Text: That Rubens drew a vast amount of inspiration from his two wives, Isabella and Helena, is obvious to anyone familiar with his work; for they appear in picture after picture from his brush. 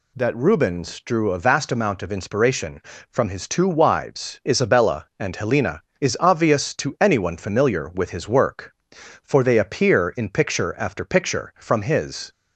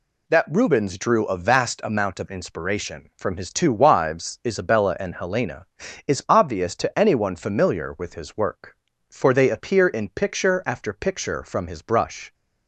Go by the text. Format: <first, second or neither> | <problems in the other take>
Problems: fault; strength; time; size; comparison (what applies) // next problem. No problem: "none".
second | stops before "brush"; at 12.3 s